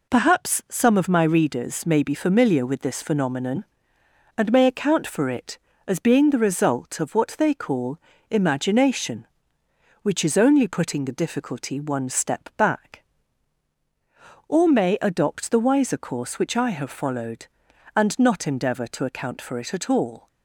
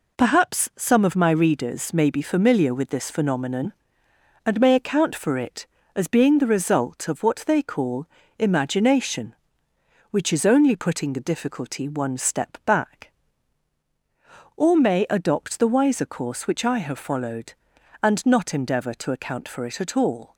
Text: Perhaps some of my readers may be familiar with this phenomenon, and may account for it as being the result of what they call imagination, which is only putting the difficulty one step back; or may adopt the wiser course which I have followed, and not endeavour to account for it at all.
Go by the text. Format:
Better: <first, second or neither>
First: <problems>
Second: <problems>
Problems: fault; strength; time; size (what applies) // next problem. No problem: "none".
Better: neither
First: pauses between "call" and "imagination"; slight; at 7.9 s; 0.32 s long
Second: pauses between "call" and "imagination"; slight; at 8.0 s; 0.32 s long